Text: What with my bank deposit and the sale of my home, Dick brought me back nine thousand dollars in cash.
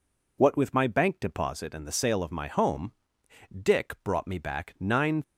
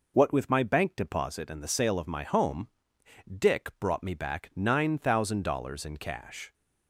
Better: second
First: stops before "thousand dollars in cash"; at 5.2 s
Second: none

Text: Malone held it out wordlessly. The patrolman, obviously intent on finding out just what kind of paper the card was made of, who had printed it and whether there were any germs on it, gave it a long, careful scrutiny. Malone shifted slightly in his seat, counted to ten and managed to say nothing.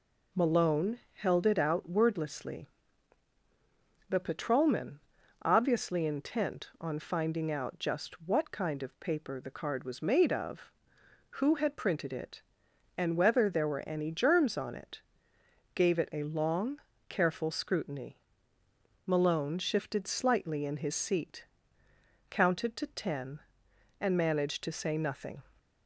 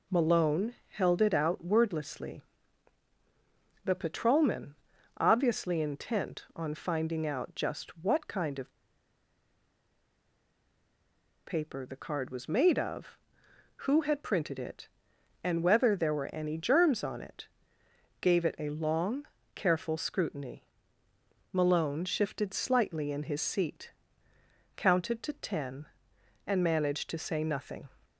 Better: first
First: none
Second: pauses between "of" and "paper"; strong; at 8.7 s; 2.7 s long

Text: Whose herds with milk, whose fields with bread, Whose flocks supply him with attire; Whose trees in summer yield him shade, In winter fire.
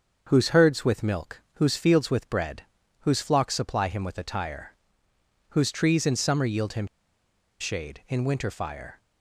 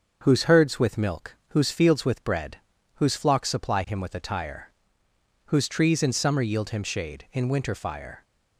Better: second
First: starts louder than the rest; until 1.2 s; 6.5 dB // pauses between "him" and "shade"; noticeable; at 6.8 s; 0.74 s long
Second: starts louder than the rest; until 1.2 s; 6.5 dB

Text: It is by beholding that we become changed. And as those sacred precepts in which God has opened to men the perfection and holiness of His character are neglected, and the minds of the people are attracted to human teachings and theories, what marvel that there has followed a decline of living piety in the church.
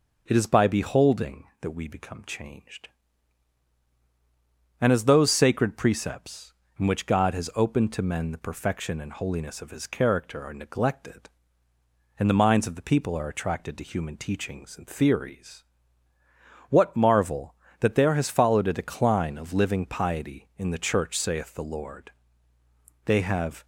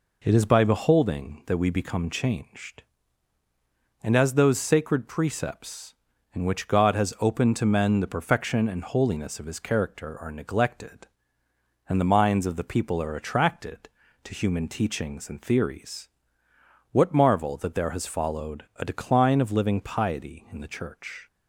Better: second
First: goes on to say "Saith the Lord They have"; strong; from 21.1 s on; 2.5 s long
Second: none

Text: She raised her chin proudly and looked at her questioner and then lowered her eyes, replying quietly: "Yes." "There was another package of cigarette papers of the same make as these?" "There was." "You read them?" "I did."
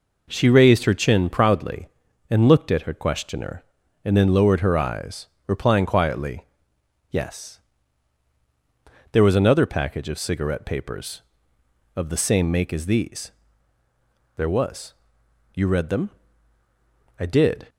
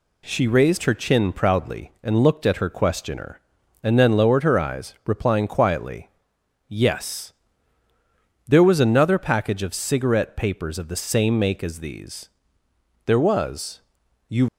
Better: first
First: none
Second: stops before "read them I did"; at 14.4 s

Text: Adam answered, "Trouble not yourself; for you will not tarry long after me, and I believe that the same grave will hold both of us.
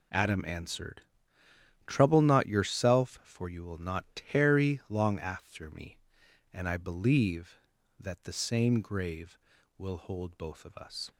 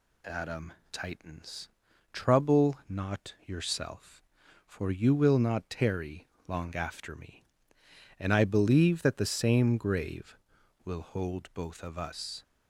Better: first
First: none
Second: says "tightens" for "answered"; at 0.9 s // pauses between "tarry" and "long"; slight; at 6.2 s; 0.20 s long

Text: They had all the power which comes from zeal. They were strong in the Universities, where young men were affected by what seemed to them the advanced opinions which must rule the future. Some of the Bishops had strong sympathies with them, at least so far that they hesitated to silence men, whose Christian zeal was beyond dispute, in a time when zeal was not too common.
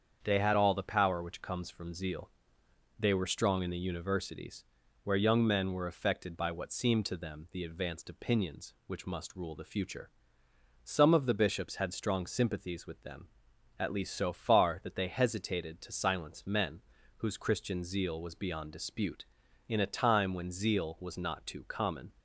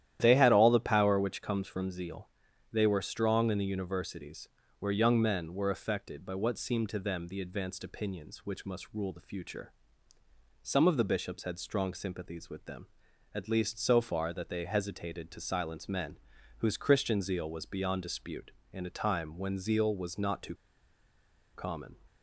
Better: first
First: starts louder than the rest; strong; until 1.2 s; 7.5 dB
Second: starts louder than the rest; strong; until 1.2 s; 11.5 dB // pauses between "too" and "common"; at 20.5 s; 0.99 s long

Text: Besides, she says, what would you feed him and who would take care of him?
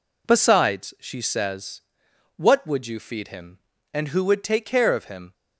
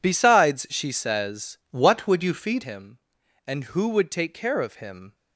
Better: first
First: none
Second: changes voice from "what" to "feed"; from 1.7 to 2.6 s; 0.9 s long

